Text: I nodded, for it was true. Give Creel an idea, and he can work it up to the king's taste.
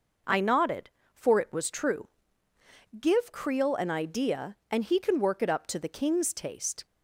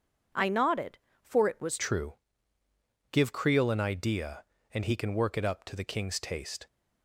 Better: first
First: none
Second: changes voice at "true"; from 1.7 s on; 4.9 s long

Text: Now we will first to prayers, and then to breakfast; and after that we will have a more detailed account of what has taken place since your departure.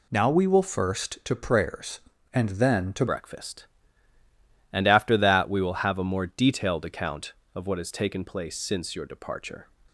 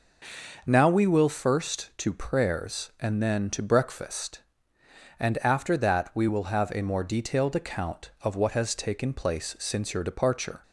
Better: second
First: changes voice at "breakfast"; from 3.0 s on; 6.6 s long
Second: none

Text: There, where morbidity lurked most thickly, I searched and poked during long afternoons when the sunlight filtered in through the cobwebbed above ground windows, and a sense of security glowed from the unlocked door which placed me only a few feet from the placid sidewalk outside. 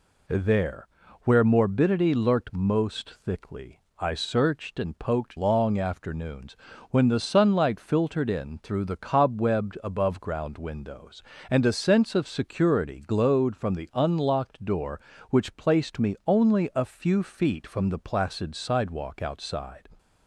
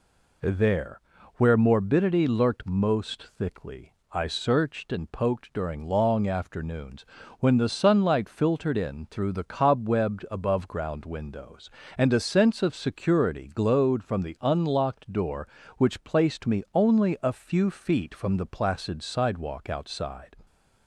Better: second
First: skips "during"; at 5.3 s // pauses between "afternoons" and "when"; slight; at 6.5 s; 0.36 s long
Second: pauses between "afternoons" and "when"; slight; at 7.0 s; 0.36 s long

